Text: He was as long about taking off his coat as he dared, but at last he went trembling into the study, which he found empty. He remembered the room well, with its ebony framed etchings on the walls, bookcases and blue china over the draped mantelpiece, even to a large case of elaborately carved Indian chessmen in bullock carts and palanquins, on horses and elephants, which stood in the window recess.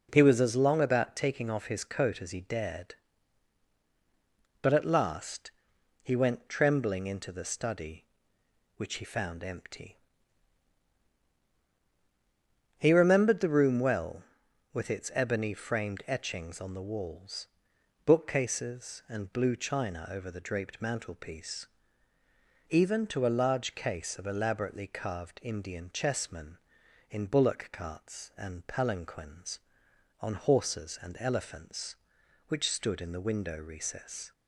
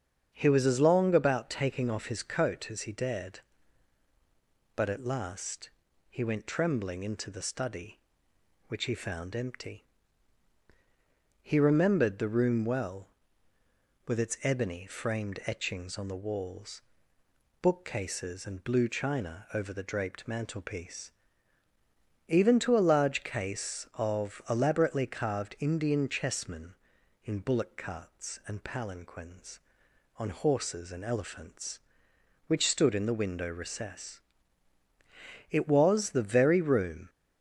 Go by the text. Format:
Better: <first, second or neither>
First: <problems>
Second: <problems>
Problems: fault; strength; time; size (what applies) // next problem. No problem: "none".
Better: first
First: pauses between "last" and "he"; noticeable; at 5.5 s; 0.50 s long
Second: starts louder than the rest; strong; until 1.3 s; 8 dB // pauses between "last" and "he"; at 5.6 s; 0.40 s long // goes on to say "It was the very room"; from 35.4 s on; 1.6 s long